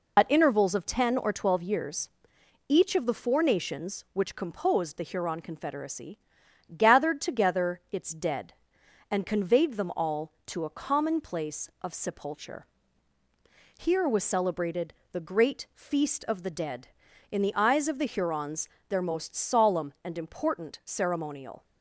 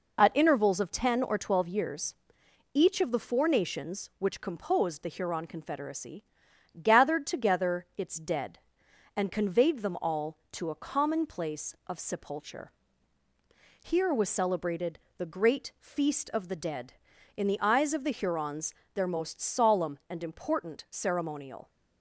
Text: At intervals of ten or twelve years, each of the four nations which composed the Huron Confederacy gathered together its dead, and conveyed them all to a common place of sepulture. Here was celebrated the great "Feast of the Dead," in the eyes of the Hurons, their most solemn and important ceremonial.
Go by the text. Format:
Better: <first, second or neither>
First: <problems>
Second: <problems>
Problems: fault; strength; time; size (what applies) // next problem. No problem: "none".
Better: second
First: loses the start of "At"; at 0.1 s; 40 ms // pauses between "Confederacy" and "gathered"; noticeable; at 6.1 s; 0.58 s long // pauses between "celebrated" and "the"; slight; at 14.9 s; 0.16 s long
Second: pauses between "Confederacy" and "gathered"; noticeable; at 6.2 s; 0.58 s long // pauses between "celebrated" and "the"; slight; at 14.9 s; 0.16 s long